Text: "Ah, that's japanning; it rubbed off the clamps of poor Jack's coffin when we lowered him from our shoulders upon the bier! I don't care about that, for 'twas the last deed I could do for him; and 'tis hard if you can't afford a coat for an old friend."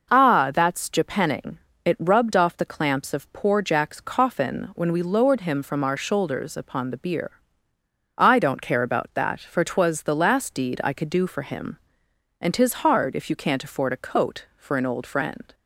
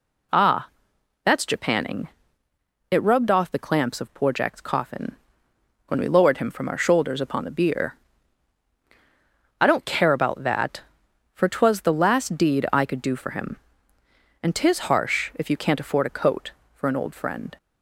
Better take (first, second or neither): first